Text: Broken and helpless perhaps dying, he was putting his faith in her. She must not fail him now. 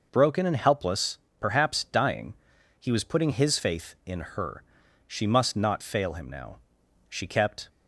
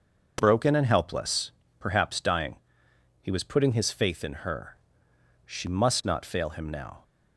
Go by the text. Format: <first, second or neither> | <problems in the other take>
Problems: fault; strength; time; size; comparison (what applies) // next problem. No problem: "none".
second | pauses between "helpless" and "perhaps"; slight; at 1.1 s; 0.22 s long; slight in the second // goes on to say "She kept"; from 7.0 s on; 0.60 s long